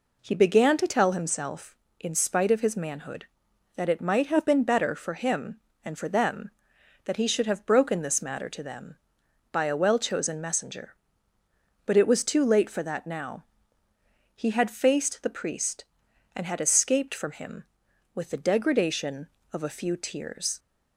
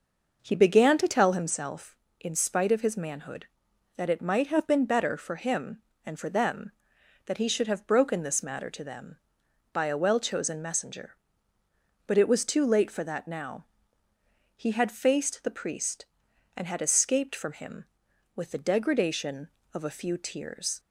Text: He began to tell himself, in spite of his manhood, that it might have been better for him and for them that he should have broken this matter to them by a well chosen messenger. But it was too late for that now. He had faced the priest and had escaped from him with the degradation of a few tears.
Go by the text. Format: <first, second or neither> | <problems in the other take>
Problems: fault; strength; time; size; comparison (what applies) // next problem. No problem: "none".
first | starts louder than the rest; noticeable; until 1.5 s; 6 dB